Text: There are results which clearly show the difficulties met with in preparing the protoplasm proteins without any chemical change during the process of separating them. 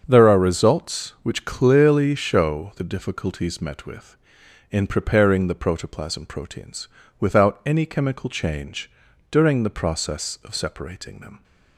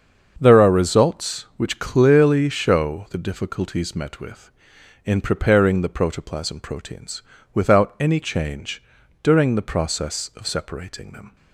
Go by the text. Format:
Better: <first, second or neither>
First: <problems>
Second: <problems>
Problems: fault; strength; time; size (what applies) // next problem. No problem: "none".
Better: first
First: starts louder than the rest; strong; until 1.0 s; 7 dB // pauses between "proteins" and "without"; slight; at 6.8 s; 0.32 s long // pauses between "change" and "during"; at 8.9 s; 0.40 s long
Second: starts louder than the rest; until 1.4 s; 7 dB // pauses between "proteins" and "without"; slight; at 7.2 s; 0.32 s long // skips "chemical"; at 8.2 s // pauses between "change" and "during"; at 8.8 s; 0.40 s long